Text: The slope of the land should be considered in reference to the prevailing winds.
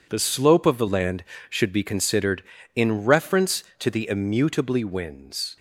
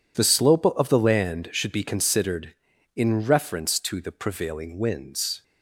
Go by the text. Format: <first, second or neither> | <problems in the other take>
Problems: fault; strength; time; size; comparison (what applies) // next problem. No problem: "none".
second | says "immutably" for "prevailing"; at 4.0 s